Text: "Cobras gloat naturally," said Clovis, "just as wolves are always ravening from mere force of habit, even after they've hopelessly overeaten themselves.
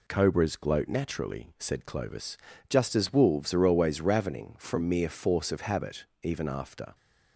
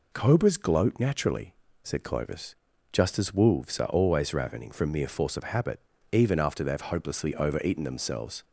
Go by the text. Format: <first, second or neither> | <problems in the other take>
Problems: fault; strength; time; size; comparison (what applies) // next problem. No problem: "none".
second | stops before "they've hopelessly overeaten themselves"; at 6.9 s